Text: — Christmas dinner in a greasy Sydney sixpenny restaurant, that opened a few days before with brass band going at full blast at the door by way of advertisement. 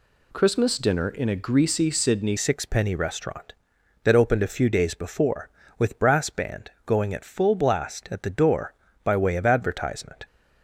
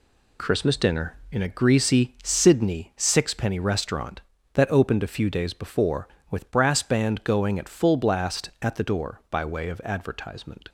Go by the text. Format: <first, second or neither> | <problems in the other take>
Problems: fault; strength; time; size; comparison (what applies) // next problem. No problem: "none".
second | changes voice at "sixpenny"; from 2.3 s on; 7.9 s long // pauses between "band" and "going"; slight; at 6.7 s; 0.16 s long